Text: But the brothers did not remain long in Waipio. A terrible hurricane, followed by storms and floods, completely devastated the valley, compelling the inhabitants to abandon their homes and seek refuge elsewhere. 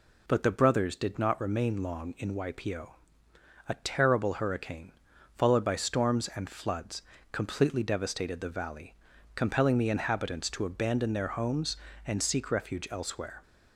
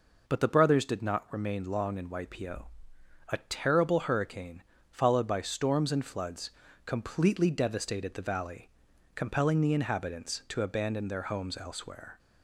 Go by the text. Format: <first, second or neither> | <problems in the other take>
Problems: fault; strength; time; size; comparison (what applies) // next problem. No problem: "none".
first | skips "and seek refuge"; at 11.5 s